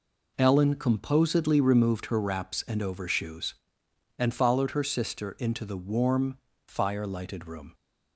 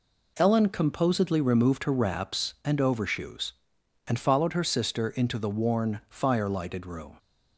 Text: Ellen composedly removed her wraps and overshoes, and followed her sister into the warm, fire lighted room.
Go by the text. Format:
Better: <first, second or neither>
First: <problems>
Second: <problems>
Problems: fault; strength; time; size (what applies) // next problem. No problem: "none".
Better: first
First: none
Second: says "worn" for "warm"; at 5.4 s